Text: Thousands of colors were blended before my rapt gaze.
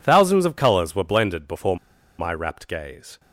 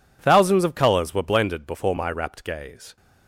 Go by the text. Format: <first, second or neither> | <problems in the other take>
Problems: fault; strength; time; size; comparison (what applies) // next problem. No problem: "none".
second | pauses between "before" and "my"; at 1.7 s; 0.41 s long